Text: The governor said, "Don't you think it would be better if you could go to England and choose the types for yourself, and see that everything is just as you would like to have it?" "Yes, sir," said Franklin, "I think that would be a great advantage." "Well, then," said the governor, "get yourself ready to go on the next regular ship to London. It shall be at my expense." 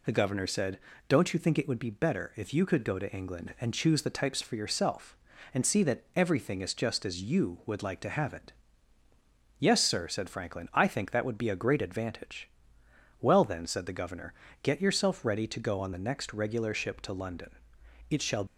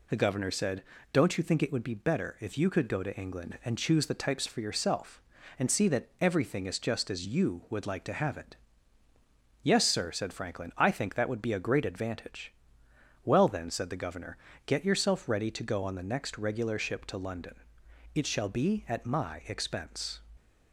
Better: second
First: stops before "be at my expense"; at 18.4 s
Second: none

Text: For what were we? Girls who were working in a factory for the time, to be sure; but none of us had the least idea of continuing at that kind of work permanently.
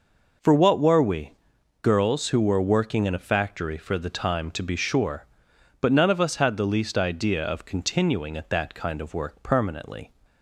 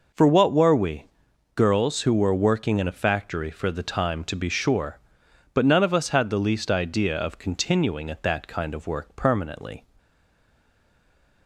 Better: first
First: none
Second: stays silent after the last word; noticeable; from 9.9 s on; 1.5 s long

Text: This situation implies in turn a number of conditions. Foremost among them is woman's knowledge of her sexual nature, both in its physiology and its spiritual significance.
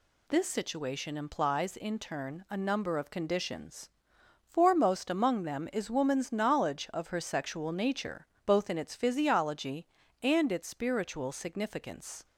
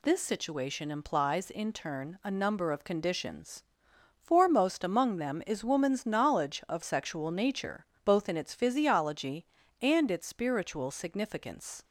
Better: first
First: none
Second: skips "her"; at 6.8 s

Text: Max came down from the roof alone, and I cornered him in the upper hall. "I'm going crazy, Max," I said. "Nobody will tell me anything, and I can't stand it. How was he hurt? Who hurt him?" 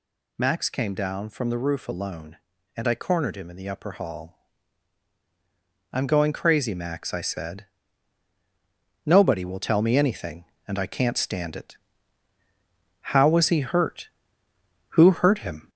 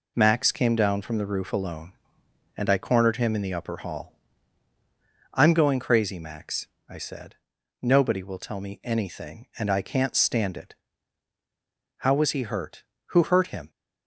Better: second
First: gets louder; noticeable; throughout; 4 dB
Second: none

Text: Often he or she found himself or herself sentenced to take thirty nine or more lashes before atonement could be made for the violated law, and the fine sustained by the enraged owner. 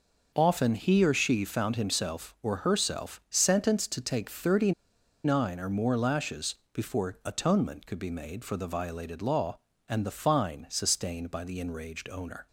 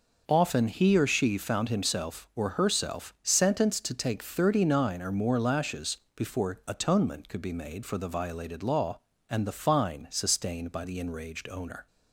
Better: second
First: pauses between "thirty" and "nine"; noticeable; at 4.7 s; 0.52 s long // pauses between "lashes" and "before"; slight; at 6.5 s; 0.18 s long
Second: pauses between "lashes" and "before"; slight; at 5.9 s; 0.18 s long

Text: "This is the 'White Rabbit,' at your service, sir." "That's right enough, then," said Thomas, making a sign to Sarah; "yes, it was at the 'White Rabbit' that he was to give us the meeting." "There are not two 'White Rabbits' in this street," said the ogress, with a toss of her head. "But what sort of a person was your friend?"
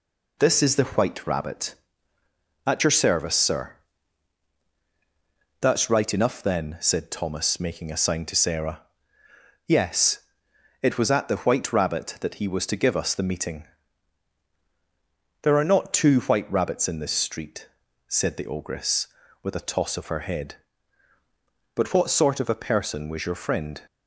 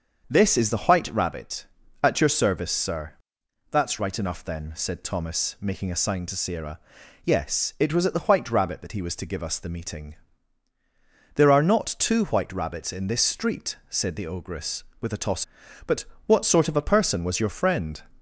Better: first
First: none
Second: starts louder than the rest; until 1.3 s; 6.5 dB // skips "of her head"; at 15.6 s // pauses between "But" and "what"; slight; at 16.0 s; 0.18 s long

